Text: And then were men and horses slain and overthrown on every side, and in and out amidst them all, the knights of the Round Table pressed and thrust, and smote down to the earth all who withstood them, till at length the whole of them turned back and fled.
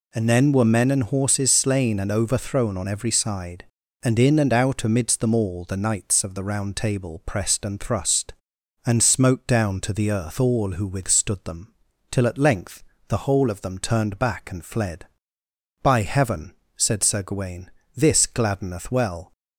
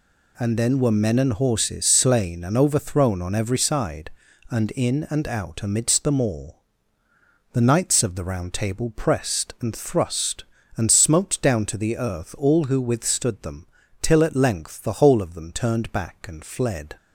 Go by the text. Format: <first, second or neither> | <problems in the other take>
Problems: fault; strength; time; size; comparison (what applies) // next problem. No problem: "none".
second | pauses between "length" and "the"; slight; at 12.8 s; 0.26 s long // goes on to say "By heaven said Sir Gawain this gladdeneth well"; strong; from 15.8 s on; 3.5 s long